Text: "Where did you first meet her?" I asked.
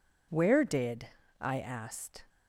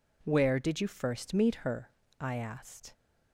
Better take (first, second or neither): second